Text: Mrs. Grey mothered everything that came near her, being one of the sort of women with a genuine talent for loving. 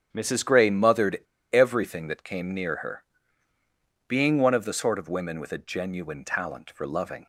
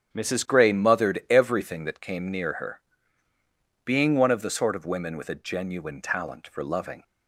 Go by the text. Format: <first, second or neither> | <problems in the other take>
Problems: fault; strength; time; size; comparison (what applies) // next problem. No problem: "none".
second | starts louder than the rest; strong; until 1.1 s; 8.5 dB; strong in the second // pauses between "mothered" and "everything"; slight; at 1.1 s; 0.35 s long